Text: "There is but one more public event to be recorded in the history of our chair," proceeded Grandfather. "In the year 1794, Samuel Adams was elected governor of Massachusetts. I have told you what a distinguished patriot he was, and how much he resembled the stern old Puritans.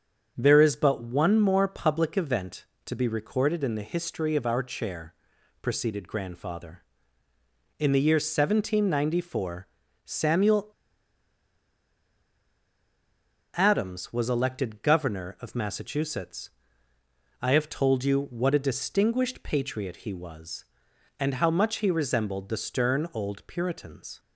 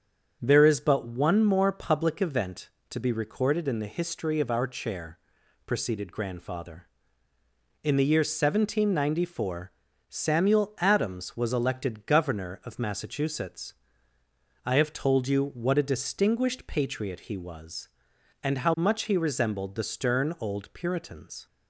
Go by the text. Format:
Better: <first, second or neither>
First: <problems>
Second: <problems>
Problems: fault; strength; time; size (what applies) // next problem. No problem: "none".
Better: second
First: starts louder than the rest; until 1.3 s; 7 dB // pauses between "Samuel" and "Adams"; strong; at 10.7 s; 2.8 s long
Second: starts louder than the rest; until 1.4 s; 7 dB